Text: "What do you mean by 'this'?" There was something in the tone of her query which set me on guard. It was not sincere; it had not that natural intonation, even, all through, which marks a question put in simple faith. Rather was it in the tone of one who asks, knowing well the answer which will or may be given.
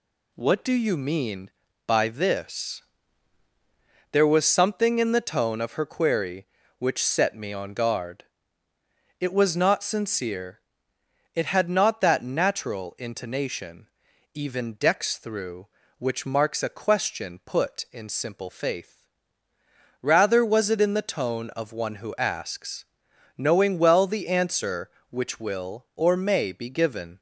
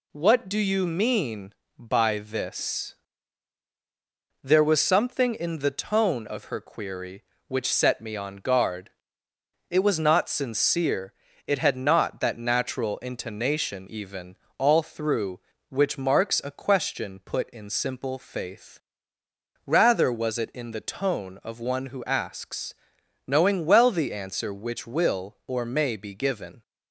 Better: second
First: says "dex" for "all"; at 14.7 s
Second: none

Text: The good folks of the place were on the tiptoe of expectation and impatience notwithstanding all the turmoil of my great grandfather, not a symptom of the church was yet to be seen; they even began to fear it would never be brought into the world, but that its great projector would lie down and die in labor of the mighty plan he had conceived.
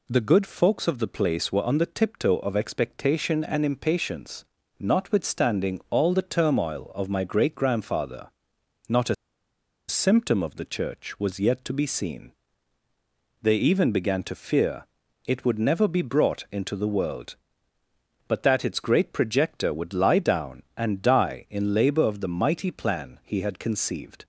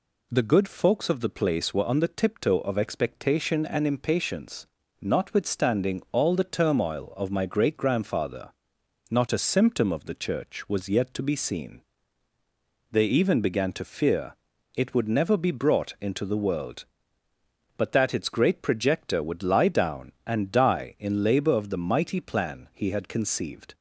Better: second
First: pauses between "impatience" and "notwithstanding"; slight; at 4.4 s; 0.34 s long // pauses between "a" and "symptom"; noticeable; at 9.1 s; 0.73 s long // pauses between "fear" and "it"; at 14.8 s; 0.40 s long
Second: pauses between "impatience" and "notwithstanding"; slight; at 4.6 s; 0.34 s long // pauses between "fear" and "it"; at 14.3 s; 0.40 s long

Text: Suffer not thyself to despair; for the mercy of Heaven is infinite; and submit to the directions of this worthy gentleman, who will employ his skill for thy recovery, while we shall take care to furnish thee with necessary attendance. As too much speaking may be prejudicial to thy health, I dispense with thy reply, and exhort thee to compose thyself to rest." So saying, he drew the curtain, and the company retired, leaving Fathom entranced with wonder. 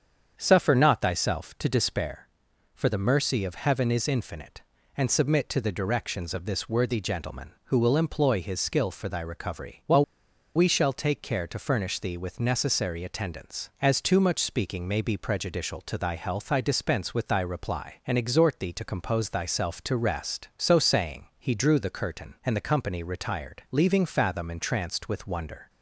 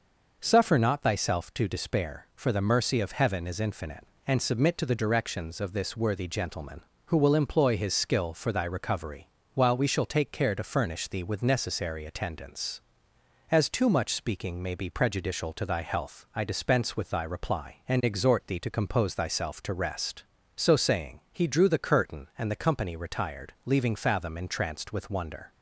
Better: second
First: starts louder than the rest; strong; until 1.3 s; 7.5 dB // pauses between "while" and "we"; noticeable; at 10.0 s; 0.51 s long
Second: none

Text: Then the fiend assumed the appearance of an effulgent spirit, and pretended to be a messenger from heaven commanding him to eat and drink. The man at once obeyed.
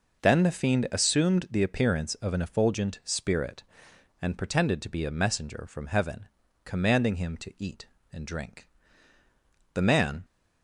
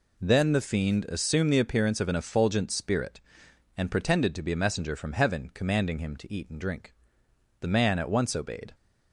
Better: second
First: pauses between "heaven" and "commanding"; at 6.2 s; 0.38 s long // stops before "at once obeyed"; at 10.2 s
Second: none

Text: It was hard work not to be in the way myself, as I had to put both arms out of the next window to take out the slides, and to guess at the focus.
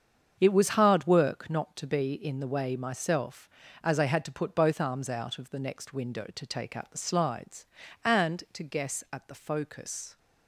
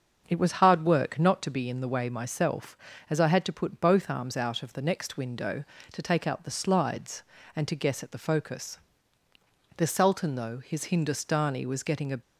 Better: first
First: starts louder than the rest; strong; until 1.4 s; 7.5 dB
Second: starts louder than the rest; until 1.2 s; 6.5 dB // goes on to say "The sultan though his Hindustani was getting a"; strong; from 9.7 s on; 2.4 s long

